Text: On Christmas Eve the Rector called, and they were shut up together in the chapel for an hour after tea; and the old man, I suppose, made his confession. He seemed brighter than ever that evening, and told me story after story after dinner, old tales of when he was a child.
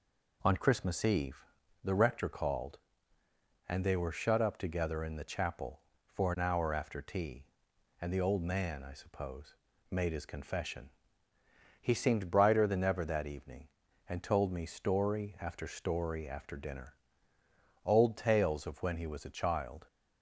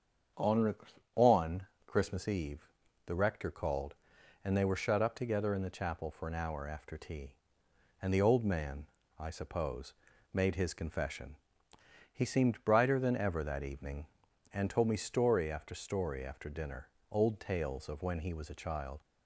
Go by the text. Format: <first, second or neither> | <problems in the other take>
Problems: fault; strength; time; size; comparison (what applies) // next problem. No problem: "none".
first | starts louder than the rest; strong; until 1.9 s; 7.5 dB // says "On" twice; at 1.1 s // pauses between "Eve" and "the"; at 2.6 s; 0.42 s long; also in the first